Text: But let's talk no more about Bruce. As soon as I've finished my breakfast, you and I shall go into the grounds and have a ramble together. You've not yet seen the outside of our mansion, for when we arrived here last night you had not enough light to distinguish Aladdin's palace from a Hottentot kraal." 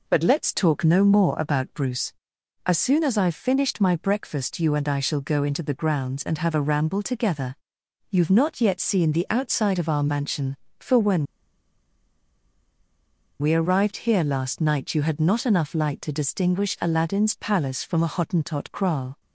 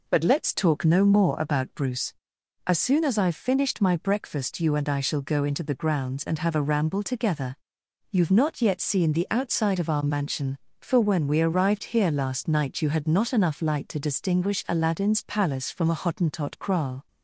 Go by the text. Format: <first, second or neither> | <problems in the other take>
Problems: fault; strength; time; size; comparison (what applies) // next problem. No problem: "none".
second | pauses between "when" and "we"; strong; at 11.2 s; 2.1 s long